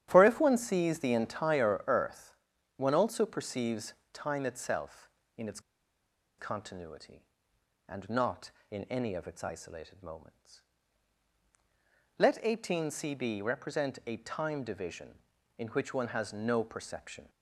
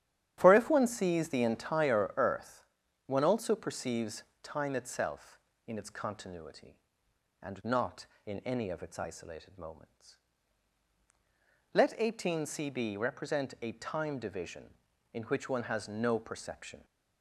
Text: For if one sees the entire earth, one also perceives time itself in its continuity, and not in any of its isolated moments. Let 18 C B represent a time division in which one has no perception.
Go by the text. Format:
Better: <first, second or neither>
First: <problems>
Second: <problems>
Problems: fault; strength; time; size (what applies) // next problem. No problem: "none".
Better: second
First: starts louder than the rest; strong; until 1.1 s; 11.5 dB // pauses between "perceives" and "time"; slight; at 3.9 s; 0.18 s long // pauses between "its" and "continuity"; noticeable; at 5.5 s; 0.78 s long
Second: starts louder than the rest; strong; until 1.3 s; 12.5 dB // pauses between "perceives" and "time"; slight; at 4.2 s; 0.18 s long